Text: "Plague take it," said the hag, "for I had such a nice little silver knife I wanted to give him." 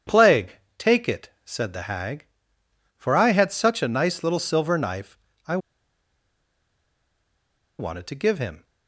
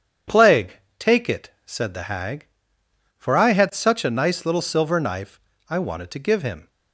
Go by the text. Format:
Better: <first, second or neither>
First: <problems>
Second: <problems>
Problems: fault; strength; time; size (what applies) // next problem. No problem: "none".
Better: second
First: starts louder than the rest; strong; until 1.2 s; 8.5 dB // pauses between "Plague" and "take"; slight; at 0.5 s; 0.20 s long // pauses between "knife" and "I"; slight; at 5.1 s; 0.28 s long // pauses between "I" and "wanted"; strong; at 5.5 s; 2.2 s long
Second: pauses between "Plague" and "take"; slight; at 0.7 s; 0.20 s long // pauses between "knife" and "I"; slight; at 5.4 s; 0.28 s long